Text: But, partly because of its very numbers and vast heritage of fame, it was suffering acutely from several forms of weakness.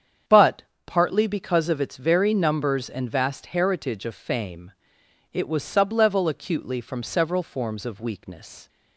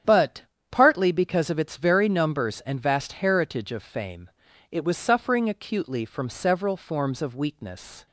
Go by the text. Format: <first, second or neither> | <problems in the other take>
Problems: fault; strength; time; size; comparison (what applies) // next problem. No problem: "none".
second | starts louder than the rest; strong; until 1.5 s; 8 dB; strong in the second // says "sublevel" for "suffering"; at 5.6 s